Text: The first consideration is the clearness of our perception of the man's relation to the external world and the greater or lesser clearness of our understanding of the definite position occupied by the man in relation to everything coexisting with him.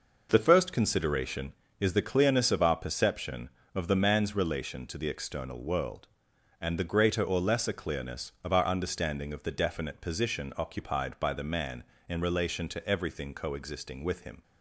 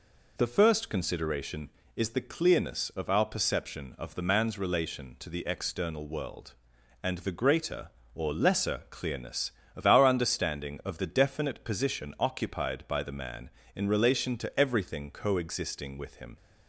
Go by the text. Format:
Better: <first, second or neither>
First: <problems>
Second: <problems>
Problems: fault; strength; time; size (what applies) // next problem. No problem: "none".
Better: neither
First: none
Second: none